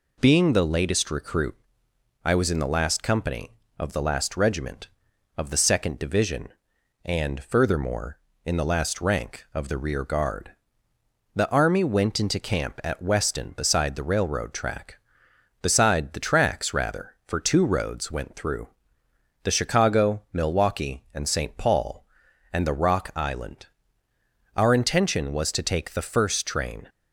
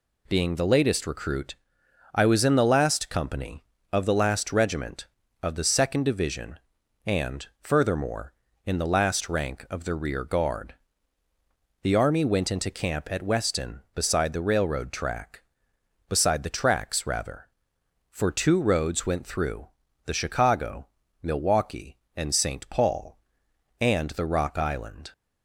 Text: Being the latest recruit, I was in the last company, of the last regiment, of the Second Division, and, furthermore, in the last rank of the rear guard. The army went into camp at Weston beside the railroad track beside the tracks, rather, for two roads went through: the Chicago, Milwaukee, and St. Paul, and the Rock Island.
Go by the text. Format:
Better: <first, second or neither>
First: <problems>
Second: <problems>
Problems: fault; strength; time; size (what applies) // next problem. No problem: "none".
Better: second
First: goes on to say "Our intention was to take the first train"; strong; from 24.5 s on; 2.3 s long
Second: none